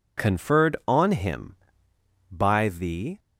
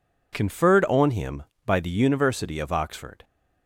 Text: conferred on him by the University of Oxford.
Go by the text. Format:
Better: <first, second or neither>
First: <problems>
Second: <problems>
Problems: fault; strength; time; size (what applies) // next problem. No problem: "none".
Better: second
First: stops before "University of Oxford"; at 3.1 s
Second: none